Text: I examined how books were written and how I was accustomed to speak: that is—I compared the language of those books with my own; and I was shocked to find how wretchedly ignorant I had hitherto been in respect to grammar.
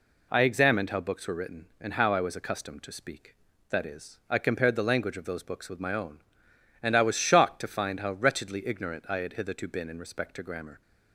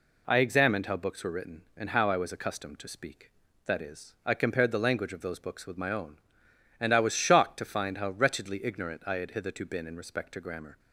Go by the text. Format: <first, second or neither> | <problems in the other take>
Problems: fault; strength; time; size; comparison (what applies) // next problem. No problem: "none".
neither | none